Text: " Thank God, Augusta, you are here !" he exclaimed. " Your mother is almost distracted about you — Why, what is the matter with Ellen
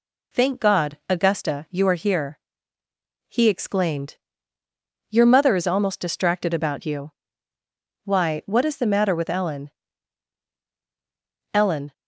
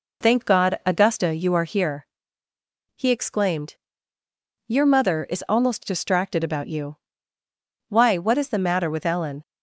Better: second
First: says "Ellen" twice; at 11.5 s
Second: none

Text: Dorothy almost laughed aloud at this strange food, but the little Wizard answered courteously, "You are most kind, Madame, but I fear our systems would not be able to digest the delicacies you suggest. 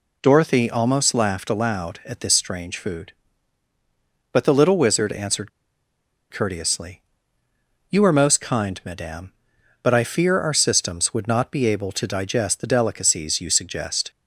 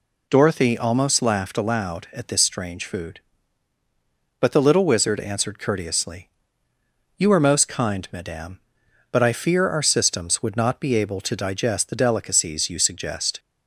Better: second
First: pauses between "answered" and "courteously"; noticeable; at 5.4 s; 0.82 s long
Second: none

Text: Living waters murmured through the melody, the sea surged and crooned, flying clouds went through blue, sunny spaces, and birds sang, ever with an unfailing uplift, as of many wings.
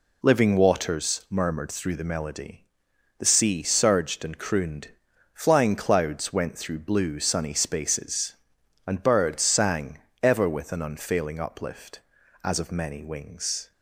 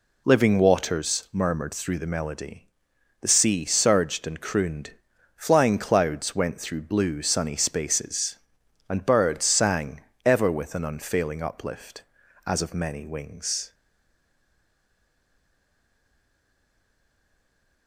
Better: first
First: none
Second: stays silent after the last word; strong; from 13.7 s on; 4.1 s long

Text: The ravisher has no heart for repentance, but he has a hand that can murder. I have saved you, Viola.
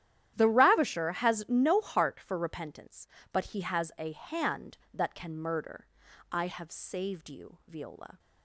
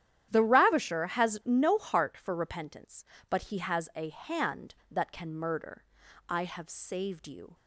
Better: first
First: starts louder than the rest; strong; until 1.3 s; 11.5 dB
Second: starts louder than the rest; strong; until 1.3 s; 11 dB // stops before "Viola"; at 7.5 s

